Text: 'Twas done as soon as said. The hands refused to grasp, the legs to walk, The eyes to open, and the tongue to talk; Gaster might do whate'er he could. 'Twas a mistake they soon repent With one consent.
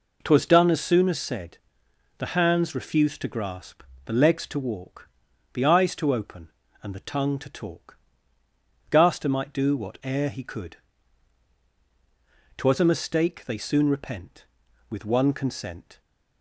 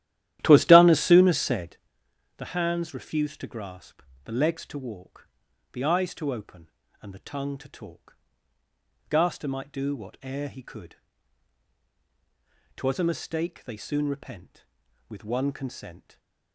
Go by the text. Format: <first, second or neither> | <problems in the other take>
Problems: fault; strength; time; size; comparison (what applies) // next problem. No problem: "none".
first | starts louder than the rest; strong; until 1.9 s; 13 dB // stays silent after the last word; slight; from 15.9 s on; 0.6 s long